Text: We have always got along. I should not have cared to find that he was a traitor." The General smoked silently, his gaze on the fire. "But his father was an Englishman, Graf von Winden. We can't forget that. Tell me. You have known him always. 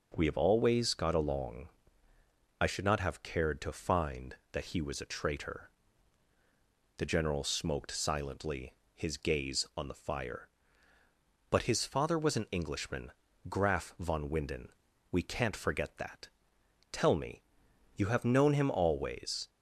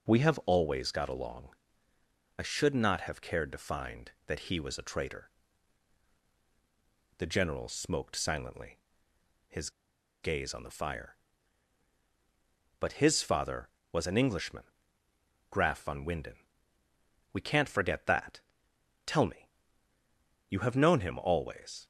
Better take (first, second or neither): first